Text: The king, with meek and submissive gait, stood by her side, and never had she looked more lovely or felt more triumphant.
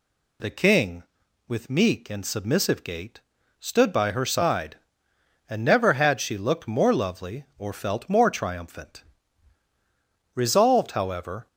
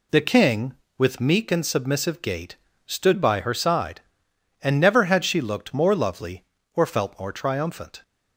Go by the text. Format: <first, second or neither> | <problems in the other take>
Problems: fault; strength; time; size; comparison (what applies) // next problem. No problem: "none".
second | goes on to say "Resolved however"; noticeable; from 10.3 s on; 1.1 s long